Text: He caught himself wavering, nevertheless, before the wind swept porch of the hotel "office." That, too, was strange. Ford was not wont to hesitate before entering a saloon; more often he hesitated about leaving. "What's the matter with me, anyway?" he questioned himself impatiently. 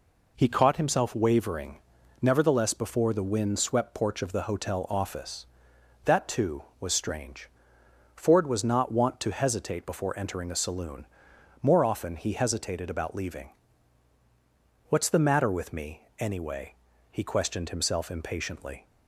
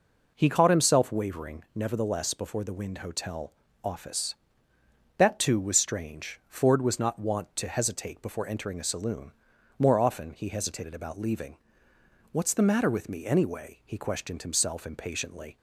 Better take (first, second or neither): first